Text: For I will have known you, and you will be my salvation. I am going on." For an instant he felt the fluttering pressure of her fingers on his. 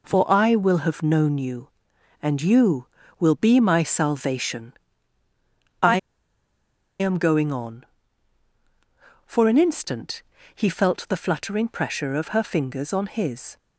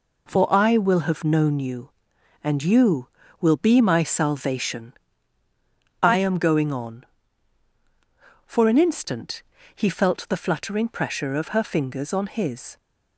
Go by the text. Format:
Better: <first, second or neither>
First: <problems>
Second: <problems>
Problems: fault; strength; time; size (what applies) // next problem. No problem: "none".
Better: second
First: pauses between "I" and "am"; at 5.9 s; 1.0 s long // pauses between "instant" and "he"; slight; at 10.2 s; 0.32 s long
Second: pauses between "instant" and "he"; slight; at 9.4 s; 0.32 s long